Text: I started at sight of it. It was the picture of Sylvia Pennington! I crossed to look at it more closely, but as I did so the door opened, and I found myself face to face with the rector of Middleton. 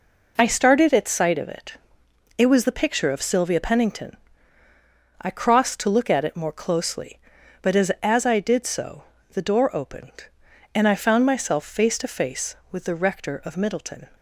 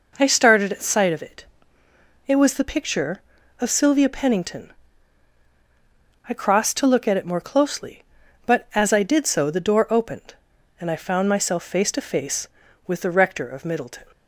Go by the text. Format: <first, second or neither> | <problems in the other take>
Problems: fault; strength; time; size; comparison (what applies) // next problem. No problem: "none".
second | says "as" twice; at 8.0 s // pauses between "so" and "the"; slight; at 9.0 s; 0.26 s long